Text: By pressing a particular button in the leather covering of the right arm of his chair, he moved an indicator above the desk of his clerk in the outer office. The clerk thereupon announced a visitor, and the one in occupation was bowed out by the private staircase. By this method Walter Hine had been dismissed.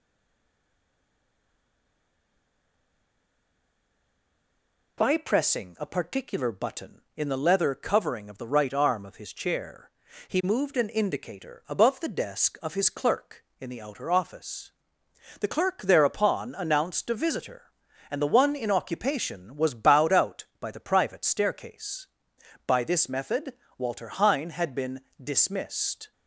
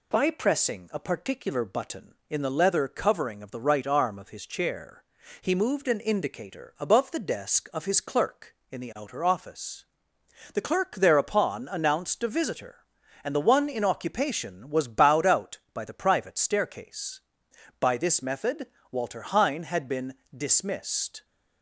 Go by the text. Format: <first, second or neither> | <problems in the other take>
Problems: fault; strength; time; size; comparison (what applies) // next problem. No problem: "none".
second | stays silent before the first word; strong; until 4.9 s; 4.9 s long // pauses between "method" and "Walter"; slight; at 23.5 s; 0.26 s long; slight in the second // pauses between "been" and "dismissed"; slight; at 25.0 s; 0.22 s long; slight in the second